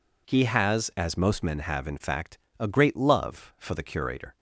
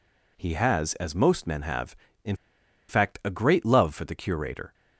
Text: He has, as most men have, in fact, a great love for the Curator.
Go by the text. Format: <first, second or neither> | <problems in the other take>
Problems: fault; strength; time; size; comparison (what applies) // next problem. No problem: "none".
first | pauses between "in" and "fact"; noticeable; at 2.3 s; 0.53 s long